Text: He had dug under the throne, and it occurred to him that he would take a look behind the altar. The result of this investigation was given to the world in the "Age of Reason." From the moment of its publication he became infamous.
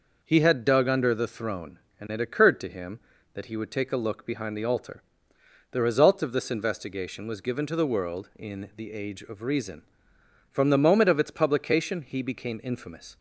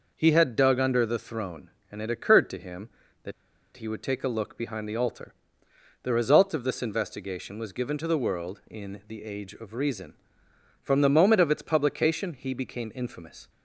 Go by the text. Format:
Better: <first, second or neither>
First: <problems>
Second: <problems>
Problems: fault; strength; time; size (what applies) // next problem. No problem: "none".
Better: first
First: none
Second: pauses between "that" and "he"; at 3.3 s; 0.44 s long